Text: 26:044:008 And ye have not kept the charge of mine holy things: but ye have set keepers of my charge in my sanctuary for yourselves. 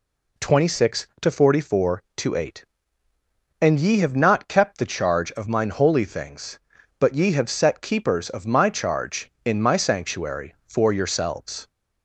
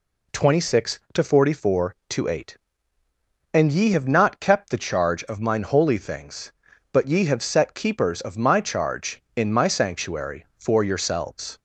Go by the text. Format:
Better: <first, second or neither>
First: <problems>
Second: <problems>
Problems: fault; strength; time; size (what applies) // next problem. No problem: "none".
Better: neither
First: none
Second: none